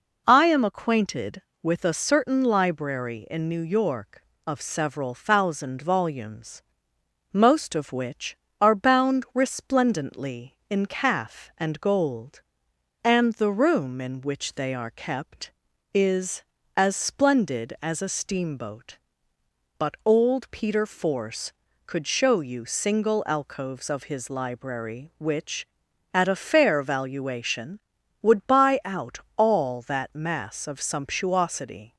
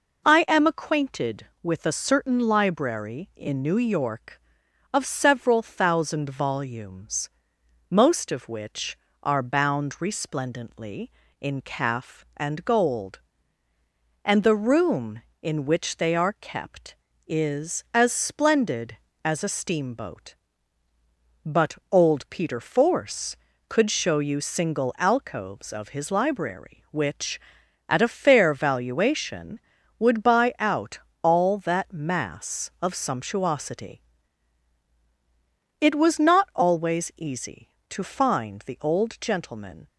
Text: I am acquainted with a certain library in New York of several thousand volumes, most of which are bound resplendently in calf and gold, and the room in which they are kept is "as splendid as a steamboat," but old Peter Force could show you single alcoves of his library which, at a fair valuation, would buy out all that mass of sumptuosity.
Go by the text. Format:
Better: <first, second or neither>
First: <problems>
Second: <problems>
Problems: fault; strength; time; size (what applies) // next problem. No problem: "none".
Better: first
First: pauses between "out" and "all"; slight; at 29.1 s; 0.18 s long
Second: pauses between "out" and "all"; slight; at 30.9 s; 0.24 s long // goes on to say "It was not always easy to find the old gentleman"; strong; from 35.7 s on; 4.0 s long